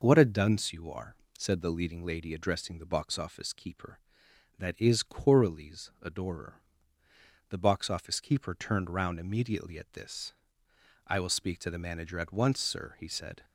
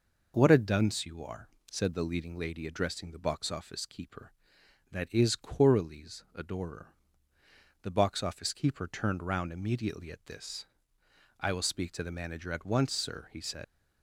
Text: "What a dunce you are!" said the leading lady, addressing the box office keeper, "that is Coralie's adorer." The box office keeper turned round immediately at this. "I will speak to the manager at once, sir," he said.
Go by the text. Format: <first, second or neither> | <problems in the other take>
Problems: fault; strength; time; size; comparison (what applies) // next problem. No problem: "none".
first | leaves "said" unfinished; at 13.6 s; 125 ms